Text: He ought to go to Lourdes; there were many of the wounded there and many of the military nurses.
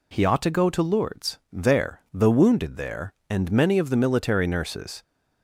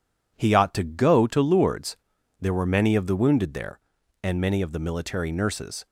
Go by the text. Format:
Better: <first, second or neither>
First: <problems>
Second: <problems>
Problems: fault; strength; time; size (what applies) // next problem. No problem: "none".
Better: second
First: skips "were many of"; at 2.0 s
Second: none